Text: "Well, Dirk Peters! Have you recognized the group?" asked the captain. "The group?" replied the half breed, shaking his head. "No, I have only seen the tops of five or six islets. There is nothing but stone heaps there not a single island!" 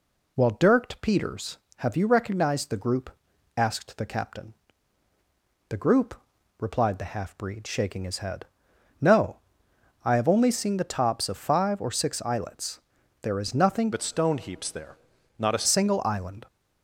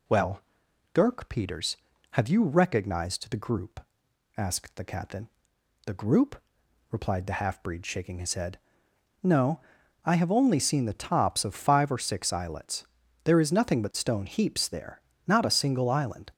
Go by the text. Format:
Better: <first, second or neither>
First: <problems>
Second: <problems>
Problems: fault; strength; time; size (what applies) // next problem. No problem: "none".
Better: second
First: changes voice from "but" to "a"; from 13.9 to 15.6 s; 1.7 s long // pauses between "there" and "not"; at 14.9 s; 0.42 s long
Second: pauses between "there" and "not"; slight; at 15.0 s; 0.24 s long